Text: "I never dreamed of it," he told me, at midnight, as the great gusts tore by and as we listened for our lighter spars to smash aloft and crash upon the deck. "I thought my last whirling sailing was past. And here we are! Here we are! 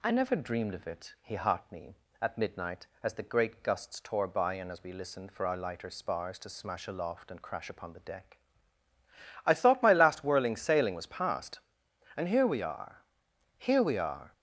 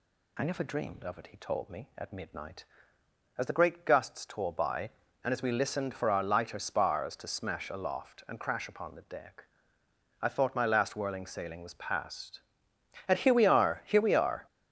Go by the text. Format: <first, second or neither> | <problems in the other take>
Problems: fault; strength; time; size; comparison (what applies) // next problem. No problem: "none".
second | says "heart" for "told"; at 1.3 s